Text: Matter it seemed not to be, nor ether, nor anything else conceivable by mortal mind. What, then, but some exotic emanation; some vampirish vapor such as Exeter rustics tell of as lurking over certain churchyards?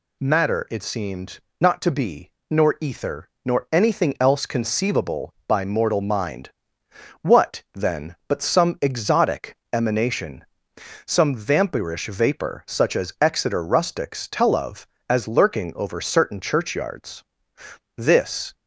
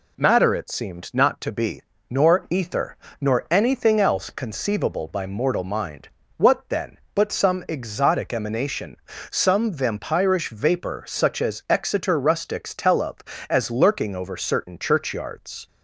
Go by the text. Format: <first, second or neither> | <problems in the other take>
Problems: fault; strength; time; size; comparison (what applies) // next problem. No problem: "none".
second | pauses between "seemed" and "not"; slight; at 1.4 s; 0.18 s long // pauses between "exotic" and "emanation"; slight; at 9.5 s; 0.16 s long // goes on to say "This"; from 17.9 s on; 0.58 s long